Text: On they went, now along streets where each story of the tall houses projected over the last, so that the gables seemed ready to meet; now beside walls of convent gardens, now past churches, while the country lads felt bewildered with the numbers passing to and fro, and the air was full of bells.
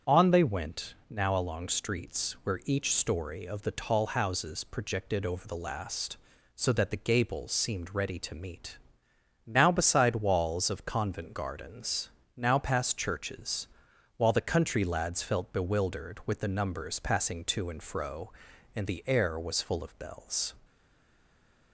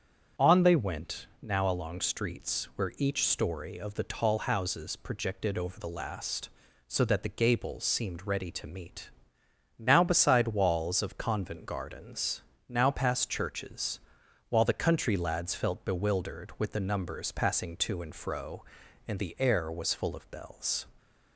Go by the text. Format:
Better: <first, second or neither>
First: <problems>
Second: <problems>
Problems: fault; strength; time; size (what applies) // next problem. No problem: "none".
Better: second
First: starts louder than the rest; strong; until 1.2 s; 7.5 dB // stays silent after the last word; from 20.6 s on; 1.1 s long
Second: starts louder than the rest; strong; until 1.5 s; 7.5 dB